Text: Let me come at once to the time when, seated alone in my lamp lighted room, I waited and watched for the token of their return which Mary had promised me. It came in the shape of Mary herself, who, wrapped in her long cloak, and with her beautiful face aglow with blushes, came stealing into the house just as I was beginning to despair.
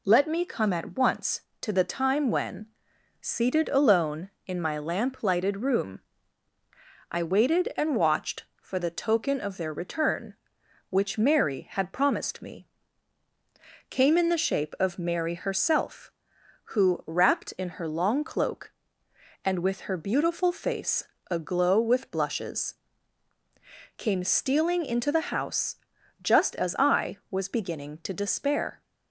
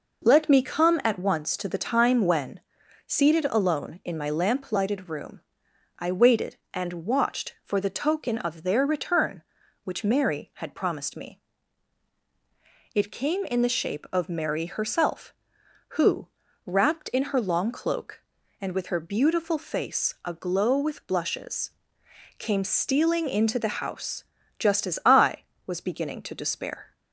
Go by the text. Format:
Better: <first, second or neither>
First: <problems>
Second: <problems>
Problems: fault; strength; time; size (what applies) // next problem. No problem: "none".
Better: second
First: skips "It"; at 13.2 s // pauses between "face" and "aglow"; slight; at 21.0 s; 0.26 s long // pauses between "house" and "just"; noticeable; at 25.7 s; 0.48 s long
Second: pauses between "house" and "just"; slight; at 24.2 s; 0.34 s long